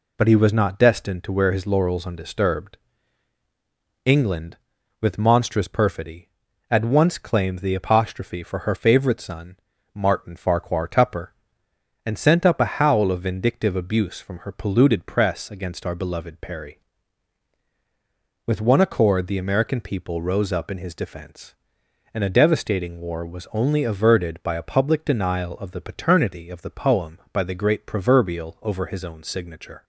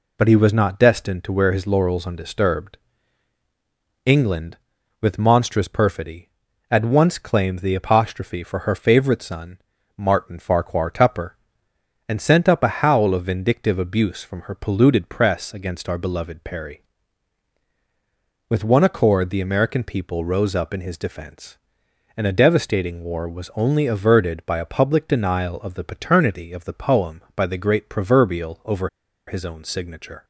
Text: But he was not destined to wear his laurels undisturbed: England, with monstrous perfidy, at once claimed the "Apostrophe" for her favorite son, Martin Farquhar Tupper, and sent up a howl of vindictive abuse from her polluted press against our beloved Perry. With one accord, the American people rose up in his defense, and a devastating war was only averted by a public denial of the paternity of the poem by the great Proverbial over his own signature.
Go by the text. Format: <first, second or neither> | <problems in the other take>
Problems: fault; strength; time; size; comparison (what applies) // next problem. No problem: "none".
first | pauses between "over" and "his"; at 28.8 s; 0.39 s long